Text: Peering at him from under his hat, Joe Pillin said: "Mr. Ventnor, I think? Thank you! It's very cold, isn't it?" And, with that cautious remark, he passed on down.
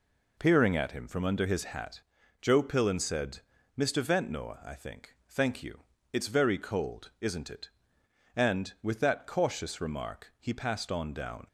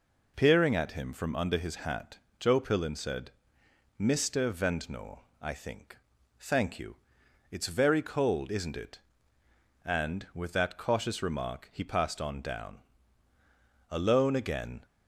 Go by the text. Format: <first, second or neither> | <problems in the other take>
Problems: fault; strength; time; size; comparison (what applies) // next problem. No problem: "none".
first | goes on to say "Alone again"; noticeable; from 13.8 s on; 0.96 s long